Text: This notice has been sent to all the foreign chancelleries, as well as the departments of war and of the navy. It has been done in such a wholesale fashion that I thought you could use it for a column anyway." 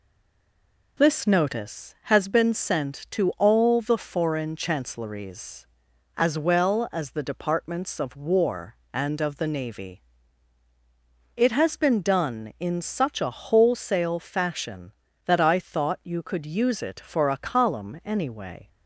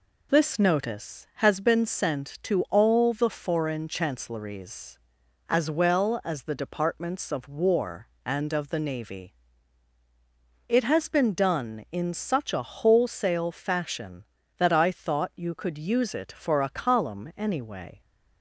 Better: second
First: stays silent before the first word; slight; until 0.9 s; 0.9 s long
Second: none

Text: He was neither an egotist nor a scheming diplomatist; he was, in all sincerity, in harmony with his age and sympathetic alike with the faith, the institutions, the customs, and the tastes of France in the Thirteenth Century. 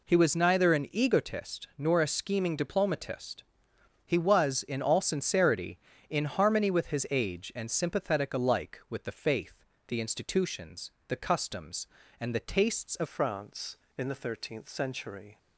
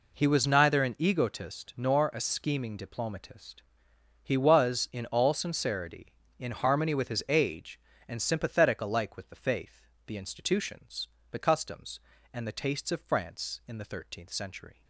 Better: second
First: changes voice at "France"; from 13.0 s on; 2.3 s long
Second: none

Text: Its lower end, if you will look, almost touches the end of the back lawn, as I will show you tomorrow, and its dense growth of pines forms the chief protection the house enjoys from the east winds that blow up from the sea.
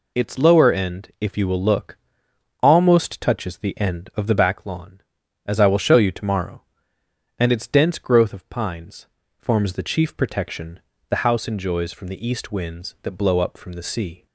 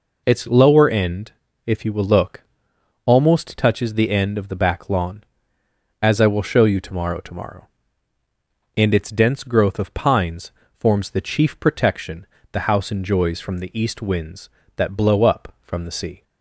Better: first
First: pauses between "pines" and "forms"; slight; at 9.0 s; 0.32 s long // pauses between "protection" and "the"; slight; at 10.7 s; 0.30 s long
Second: says "tomorrow" twice; at 7.1 s // pauses between "pines" and "forms"; slight; at 10.5 s; 0.28 s long // pauses between "protection" and "the"; slight; at 12.2 s; 0.28 s long

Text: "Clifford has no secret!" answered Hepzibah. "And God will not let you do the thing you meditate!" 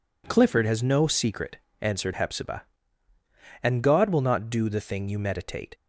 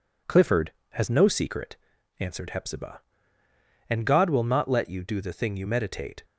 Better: second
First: skips "let you"; at 4.4 s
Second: none

